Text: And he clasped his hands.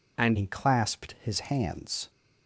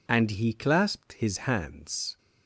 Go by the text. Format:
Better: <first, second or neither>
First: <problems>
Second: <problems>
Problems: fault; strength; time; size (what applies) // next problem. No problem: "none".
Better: second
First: changes voice at "he"; from 0.3 s on; 1.7 s long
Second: none